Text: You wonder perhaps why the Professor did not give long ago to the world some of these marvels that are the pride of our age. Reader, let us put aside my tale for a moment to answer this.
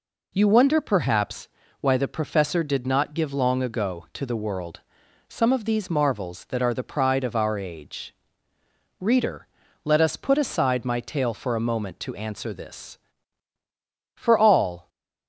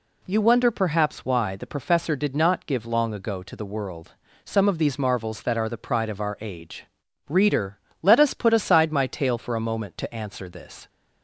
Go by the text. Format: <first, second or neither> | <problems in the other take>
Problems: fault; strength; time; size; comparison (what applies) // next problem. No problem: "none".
second | pauses between "perhaps" and "why"; slight; at 1.4 s; 0.34 s long // pauses between "world" and "some"; noticeable; at 4.8 s; 0.48 s long; slight in the second // goes on to say "For all"; noticeable; from 14.1 s on; 0.74 s long